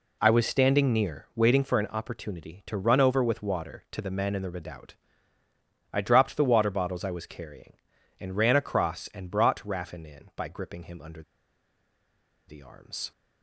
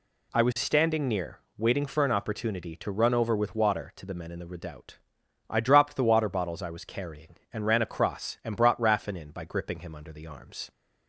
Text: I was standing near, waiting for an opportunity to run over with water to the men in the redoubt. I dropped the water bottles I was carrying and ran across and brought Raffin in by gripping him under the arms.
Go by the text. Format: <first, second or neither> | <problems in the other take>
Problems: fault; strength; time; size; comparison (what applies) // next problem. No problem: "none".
second | pauses between "under" and "the"; strong; at 11.2 s; 1.2 s long